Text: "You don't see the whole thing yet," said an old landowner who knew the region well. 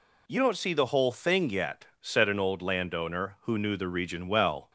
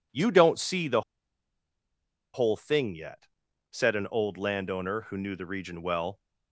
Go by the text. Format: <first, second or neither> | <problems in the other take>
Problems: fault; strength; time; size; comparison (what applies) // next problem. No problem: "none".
first | pauses between "the" and "whole"; strong; at 1.0 s; 1.3 s long